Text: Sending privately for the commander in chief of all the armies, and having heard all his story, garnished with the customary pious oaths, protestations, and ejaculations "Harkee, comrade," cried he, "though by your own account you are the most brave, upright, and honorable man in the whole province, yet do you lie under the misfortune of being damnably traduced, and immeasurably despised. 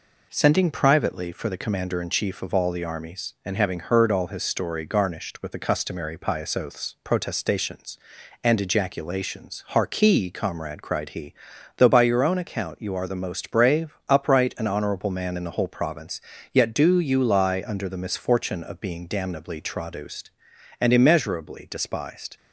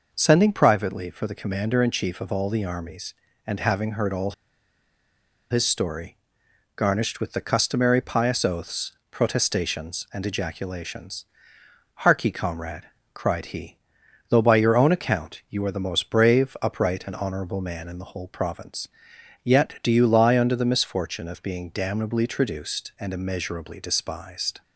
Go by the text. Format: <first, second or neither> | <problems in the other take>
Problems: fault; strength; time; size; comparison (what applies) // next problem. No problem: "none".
first | pauses between "all" and "his"; at 4.3 s; 1.1 s long // pauses between "ejaculations" and "Harkee"; noticeable; at 11.2 s; 0.78 s long